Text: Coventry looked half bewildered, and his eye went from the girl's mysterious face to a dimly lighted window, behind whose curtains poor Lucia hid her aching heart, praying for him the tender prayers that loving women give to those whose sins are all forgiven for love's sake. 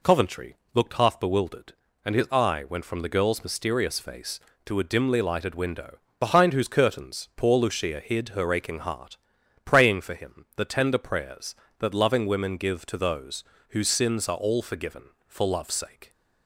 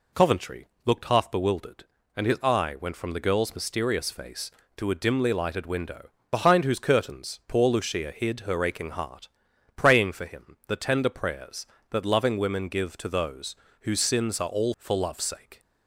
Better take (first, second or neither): first